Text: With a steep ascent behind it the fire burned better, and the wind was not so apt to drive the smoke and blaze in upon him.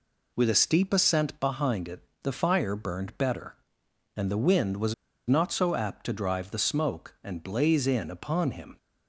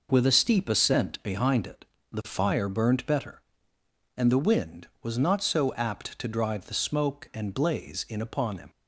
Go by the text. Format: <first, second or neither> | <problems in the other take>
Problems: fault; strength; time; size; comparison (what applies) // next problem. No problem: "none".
second | pauses between "it" and "the"; slight; at 2.0 s; 0.22 s long; slight in the second // pauses between "was" and "not"; slight; at 4.9 s; 0.34 s long